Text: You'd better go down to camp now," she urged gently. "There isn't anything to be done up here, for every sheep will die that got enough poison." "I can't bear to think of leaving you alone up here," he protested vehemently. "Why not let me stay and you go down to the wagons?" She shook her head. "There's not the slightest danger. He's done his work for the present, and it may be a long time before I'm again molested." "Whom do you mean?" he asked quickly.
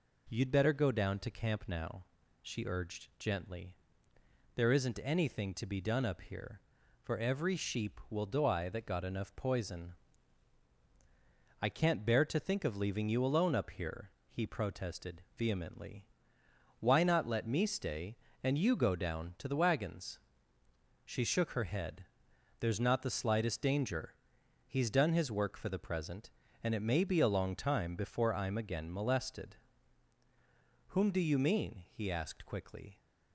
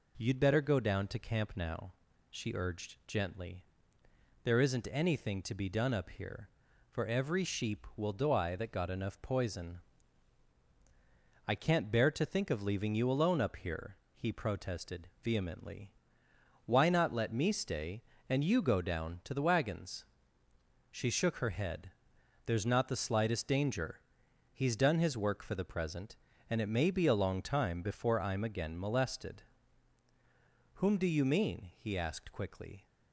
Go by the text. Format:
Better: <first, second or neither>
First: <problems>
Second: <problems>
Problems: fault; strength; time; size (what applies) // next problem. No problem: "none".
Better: neither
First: pauses between "protested" and "vehemently"; slight; at 15.2 s; 0.16 s long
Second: pauses between "protested" and "vehemently"; slight; at 15.0 s; 0.16 s long